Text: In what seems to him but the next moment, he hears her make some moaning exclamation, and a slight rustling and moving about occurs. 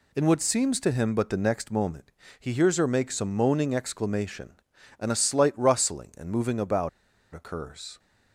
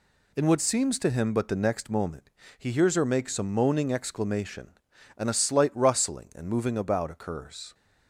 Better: second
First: pauses between "about" and "occurs"; at 6.8 s; 0.45 s long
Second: none

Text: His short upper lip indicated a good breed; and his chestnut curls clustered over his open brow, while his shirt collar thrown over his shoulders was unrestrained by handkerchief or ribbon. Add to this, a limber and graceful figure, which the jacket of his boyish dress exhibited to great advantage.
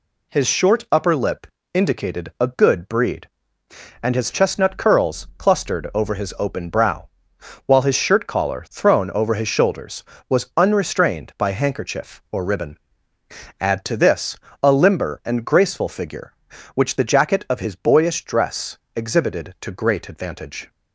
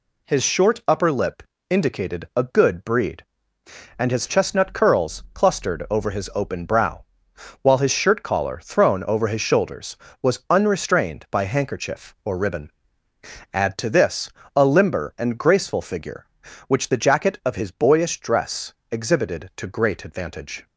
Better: neither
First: pauses between "lip" and "indicated"; slight; at 1.4 s; 0.26 s long // pauses between "dress" and "exhibited"; slight; at 18.7 s; 0.18 s long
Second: pauses between "lip" and "indicated"; slight; at 1.4 s; 0.26 s long // pauses between "dress" and "exhibited"; slight; at 18.7 s; 0.18 s long

